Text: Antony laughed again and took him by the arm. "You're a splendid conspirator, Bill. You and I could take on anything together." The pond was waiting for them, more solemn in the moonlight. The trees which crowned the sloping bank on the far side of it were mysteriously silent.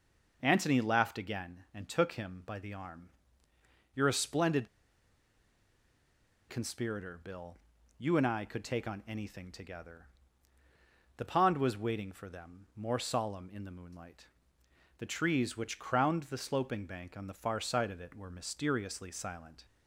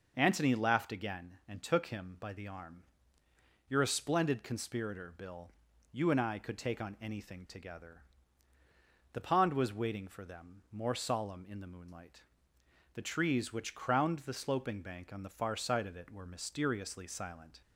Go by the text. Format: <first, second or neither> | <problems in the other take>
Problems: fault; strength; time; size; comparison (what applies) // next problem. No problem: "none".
second | pauses between "splendid" and "conspirator"; strong; at 4.6 s; 1.8 s long